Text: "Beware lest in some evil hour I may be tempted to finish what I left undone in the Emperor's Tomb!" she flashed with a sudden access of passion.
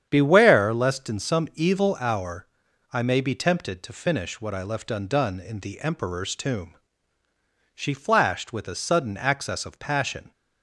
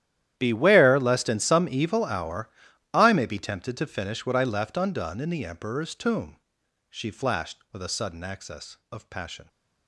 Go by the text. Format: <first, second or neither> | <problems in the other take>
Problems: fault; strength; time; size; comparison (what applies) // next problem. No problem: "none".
first | gets quieter; strong; throughout; 18 dB // starts louder than the rest; strong; until 1.3 s; 11.5 dB; strong in the first // pauses between "hour" and "I"; at 2.4 s; 0.42 s long; noticeable in the first